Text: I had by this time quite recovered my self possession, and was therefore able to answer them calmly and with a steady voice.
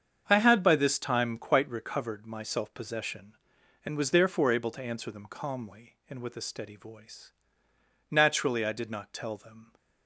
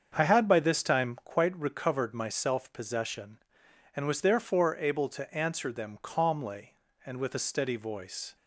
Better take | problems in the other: second | starts louder than the rest; strong; until 1.2 s; 7.5 dB; also in the second // goes on to say "Naturally I did not tell them"; from 8.0 s on; 1.6 s long

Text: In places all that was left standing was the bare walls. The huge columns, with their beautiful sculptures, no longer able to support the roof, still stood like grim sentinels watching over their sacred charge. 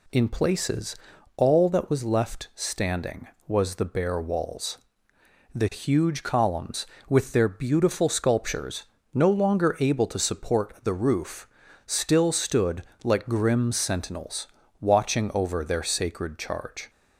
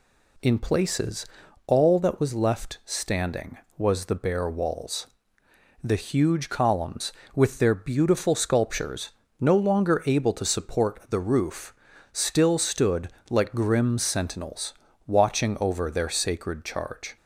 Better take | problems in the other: neither | pauses between "places" and "all"; the same in both // pauses between "stood" and "like"; slight; the same in both // pauses between "sentinels" and "watching"; slight; the same in both

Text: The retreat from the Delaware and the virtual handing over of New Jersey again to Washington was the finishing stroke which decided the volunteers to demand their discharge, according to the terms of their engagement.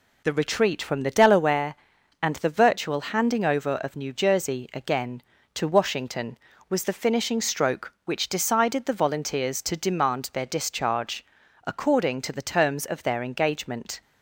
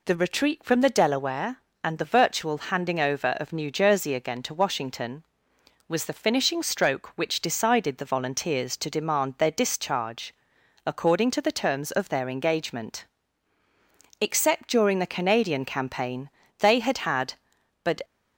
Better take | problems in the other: first | goes on to say "Except during the Canadian campaign they had had but"; strong; from 14.1 s on; 3.8 s long

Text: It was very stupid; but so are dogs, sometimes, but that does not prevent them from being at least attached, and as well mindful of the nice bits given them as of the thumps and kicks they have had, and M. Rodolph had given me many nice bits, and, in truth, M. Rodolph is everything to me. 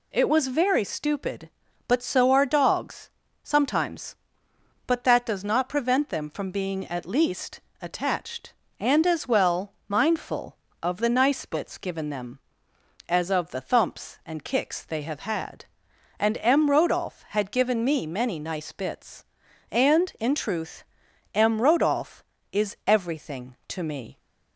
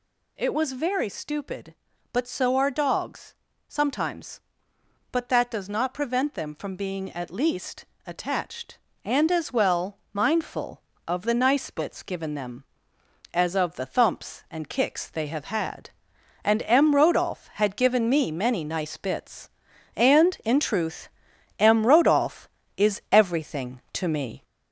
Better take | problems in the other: first | gets louder; throughout; 4 dB // pauses between "least" and "attached"; slight; at 7.8 s; 0.20 s long; slight in the first // pauses between "well" and "mindful"; slight; at 9.9 s; 0.16 s long; slight in the first

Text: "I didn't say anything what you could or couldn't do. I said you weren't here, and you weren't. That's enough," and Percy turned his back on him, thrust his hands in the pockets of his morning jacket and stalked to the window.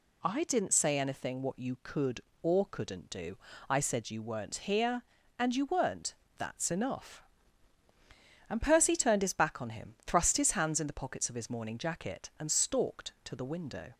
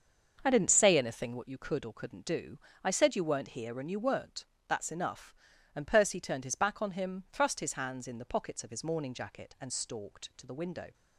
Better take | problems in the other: first | starts louder than the rest; until 1.5 s; 6.5 dB

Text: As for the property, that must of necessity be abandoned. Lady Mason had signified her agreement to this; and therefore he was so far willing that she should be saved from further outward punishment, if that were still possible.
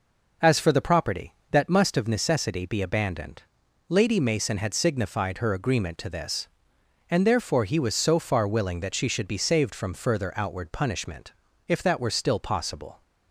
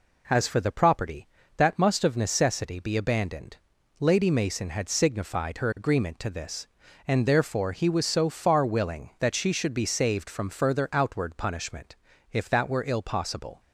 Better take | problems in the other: first | says "ill" for "still"; at 12.8 s

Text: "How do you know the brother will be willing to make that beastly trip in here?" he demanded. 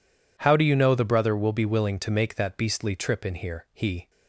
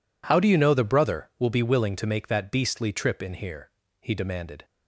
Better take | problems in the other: second | stops before "demanded"; at 4.0 s

